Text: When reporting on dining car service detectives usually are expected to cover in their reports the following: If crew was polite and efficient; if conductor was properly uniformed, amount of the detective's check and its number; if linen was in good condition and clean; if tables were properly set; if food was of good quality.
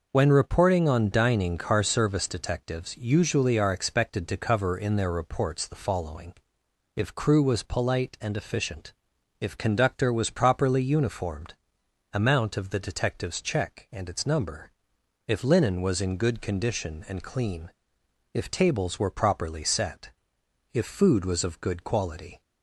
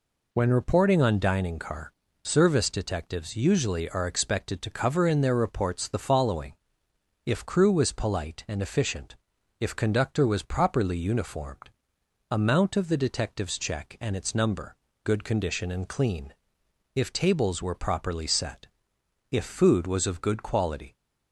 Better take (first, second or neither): first